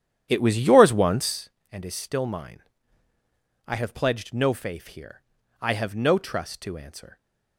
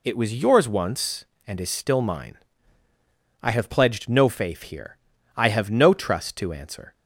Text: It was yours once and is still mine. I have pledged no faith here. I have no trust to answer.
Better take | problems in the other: second | starts louder than the rest; strong; until 1.4 s; 10.5 dB

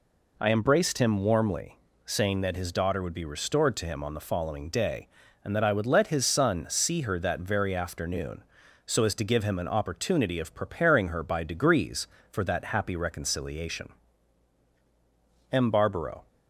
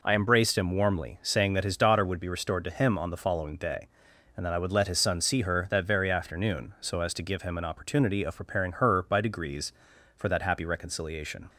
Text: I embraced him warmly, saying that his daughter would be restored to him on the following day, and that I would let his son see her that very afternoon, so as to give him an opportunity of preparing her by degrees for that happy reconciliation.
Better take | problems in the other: second | goes on to say "M Barbaro"; noticeable; from 15.5 s on; 0.76 s long

